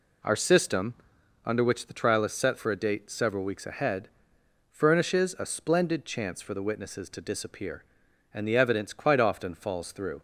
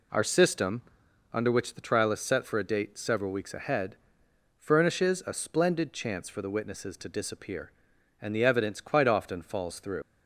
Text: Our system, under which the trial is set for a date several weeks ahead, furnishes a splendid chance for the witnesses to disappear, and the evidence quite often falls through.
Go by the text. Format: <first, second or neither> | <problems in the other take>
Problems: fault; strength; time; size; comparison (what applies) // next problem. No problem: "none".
first | leaves "through" unfinished; at 10.0 s; 55 ms